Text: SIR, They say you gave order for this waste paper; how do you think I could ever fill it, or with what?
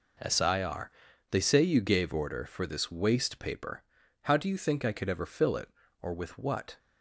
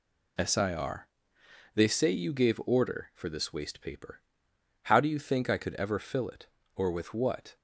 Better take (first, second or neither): second